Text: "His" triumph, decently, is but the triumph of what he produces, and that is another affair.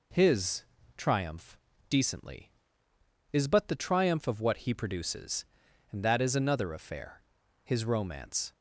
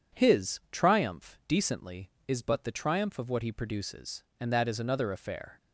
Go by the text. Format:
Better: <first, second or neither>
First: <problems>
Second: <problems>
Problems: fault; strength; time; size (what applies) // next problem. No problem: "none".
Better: second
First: pauses between "His" and "triumph"; slight; at 0.6 s; 0.34 s long // goes on to say "His romance"; noticeable; from 7.6 s on; 0.88 s long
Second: none